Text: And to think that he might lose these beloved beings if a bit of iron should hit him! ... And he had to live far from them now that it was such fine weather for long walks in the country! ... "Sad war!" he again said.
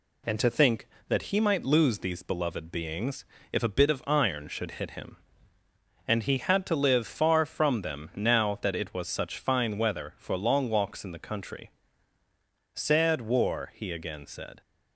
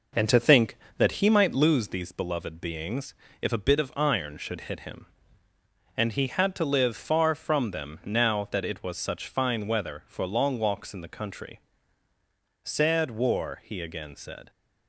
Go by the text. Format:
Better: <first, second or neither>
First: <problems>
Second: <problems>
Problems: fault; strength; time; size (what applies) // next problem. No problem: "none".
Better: first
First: pauses between "beings" and "if"; slight; at 3.2 s; 0.28 s long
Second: starts louder than the rest; noticeable; until 1.7 s; 5 dB // pauses between "beings" and "if"; slight; at 3.1 s; 0.28 s long